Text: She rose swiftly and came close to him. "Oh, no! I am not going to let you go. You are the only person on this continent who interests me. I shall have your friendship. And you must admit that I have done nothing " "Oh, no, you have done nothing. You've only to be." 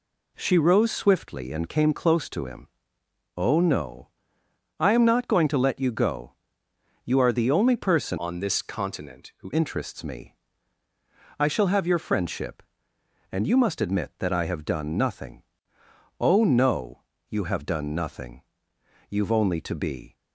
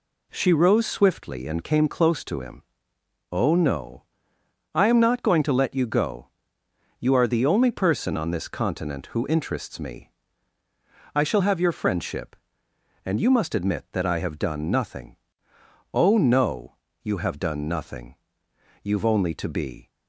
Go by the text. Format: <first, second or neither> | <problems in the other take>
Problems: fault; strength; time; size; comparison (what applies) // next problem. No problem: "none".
second | changes voice from "on" to "who"; from 8.1 to 9.5 s; 1.4 s long